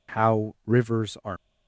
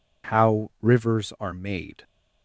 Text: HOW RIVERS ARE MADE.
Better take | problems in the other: second | stops before "MADE"; at 1.3 s

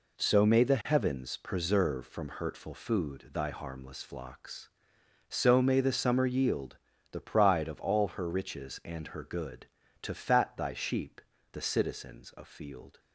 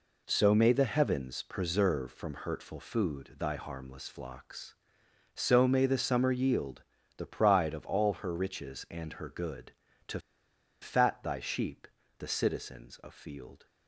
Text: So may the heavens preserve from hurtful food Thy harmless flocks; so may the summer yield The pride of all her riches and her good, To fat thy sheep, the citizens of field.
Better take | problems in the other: first | pauses between "yield" and "The"; slight; at 6.8 s; 0.36 s long; slight in the first // pauses between "To" and "fat"; noticeable; at 10.1 s; 0.63 s long

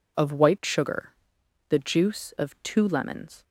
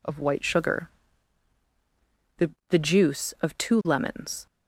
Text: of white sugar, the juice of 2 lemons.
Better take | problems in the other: first | says "the" twice; at 2.6 s

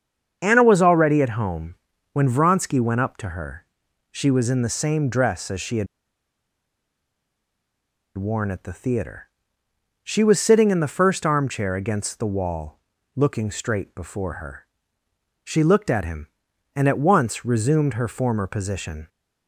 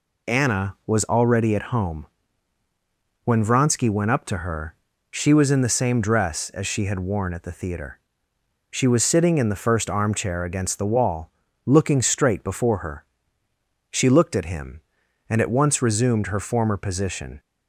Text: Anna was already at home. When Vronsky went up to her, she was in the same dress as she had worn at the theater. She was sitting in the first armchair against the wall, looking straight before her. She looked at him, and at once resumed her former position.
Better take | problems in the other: second | starts louder than the rest; strong; until 1.4 s; 7 dB // pauses between "had" and "worn"; strong; at 5.8 s; 2.3 s long

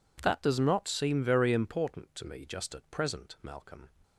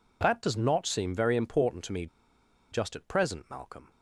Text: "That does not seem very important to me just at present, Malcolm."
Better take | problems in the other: first | pauses between "me" and "just"; noticeable; at 2.0 s; 0.66 s long

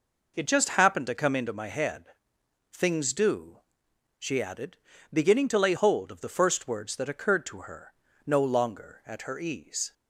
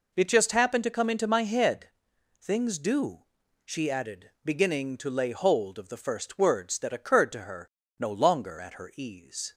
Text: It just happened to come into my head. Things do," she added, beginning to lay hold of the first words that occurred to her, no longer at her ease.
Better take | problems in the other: neither | none

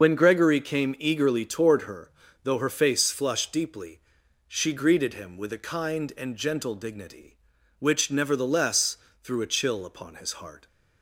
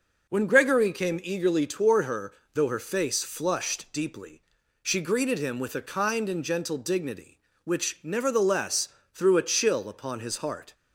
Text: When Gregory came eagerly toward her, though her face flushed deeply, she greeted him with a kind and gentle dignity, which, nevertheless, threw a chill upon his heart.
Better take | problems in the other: second | loses the start of "When"; at 0.0 s; 60 ms // starts louder than the rest; noticeable; until 1.0 s; 6 dB

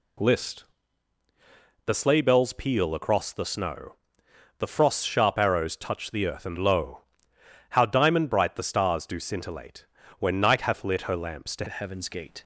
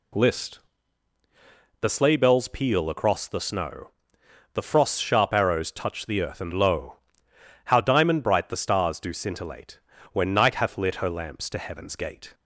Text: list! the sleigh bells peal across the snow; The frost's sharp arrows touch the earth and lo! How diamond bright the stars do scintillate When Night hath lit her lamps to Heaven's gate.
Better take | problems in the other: second | pauses between "scintillate" and "When"; slight; at 9.8 s; 0.34 s long; slight in the second // changes voice at "Heaven's"; from 11.6 s on; 0.8 s long

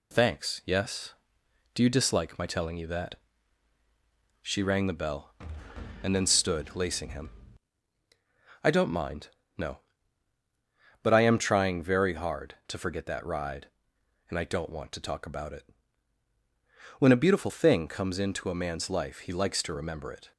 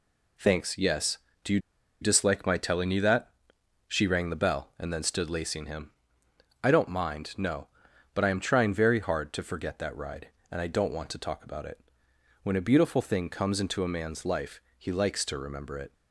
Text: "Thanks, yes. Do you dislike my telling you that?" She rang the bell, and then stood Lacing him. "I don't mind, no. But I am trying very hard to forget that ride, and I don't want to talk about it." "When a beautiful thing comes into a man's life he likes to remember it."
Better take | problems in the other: first | pauses between "you" and "dislike"; at 1.5 s; 0.42 s long // pauses between "life" and "he"; slight; at 14.6 s; 0.16 s long

